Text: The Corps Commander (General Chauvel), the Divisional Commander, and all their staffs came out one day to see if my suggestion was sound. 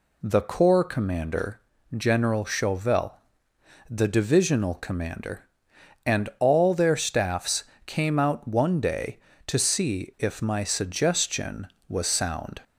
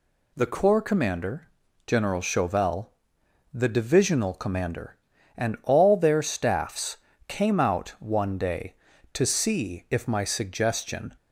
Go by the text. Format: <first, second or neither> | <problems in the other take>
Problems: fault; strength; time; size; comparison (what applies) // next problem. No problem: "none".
first | pauses between "staffs" and "came"; slight; at 6.9 s; 0.30 s long; slight in the first // stops before "was sound"; at 11.1 s